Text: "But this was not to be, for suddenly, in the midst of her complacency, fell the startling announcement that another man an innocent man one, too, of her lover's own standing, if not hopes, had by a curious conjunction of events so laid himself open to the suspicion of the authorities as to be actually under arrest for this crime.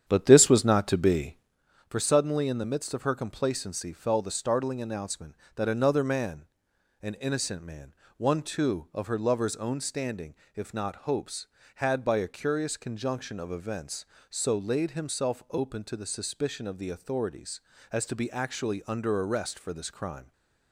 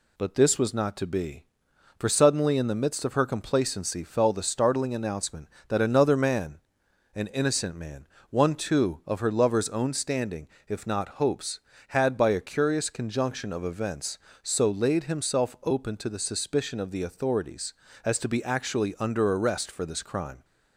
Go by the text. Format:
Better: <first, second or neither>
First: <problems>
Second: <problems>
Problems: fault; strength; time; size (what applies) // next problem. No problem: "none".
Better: second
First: starts louder than the rest; strong; until 1.6 s; 9 dB // pauses between "man" and "an"; noticeable; at 6.4 s; 0.56 s long // pauses between "man" and "one"; slight; at 7.9 s; 0.22 s long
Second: pauses between "man" and "an"; noticeable; at 6.5 s; 0.56 s long // pauses between "man" and "one"; slight; at 8.0 s; 0.22 s long